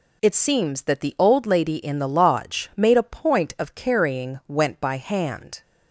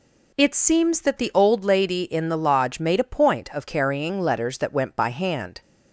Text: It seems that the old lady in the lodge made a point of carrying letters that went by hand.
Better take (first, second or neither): second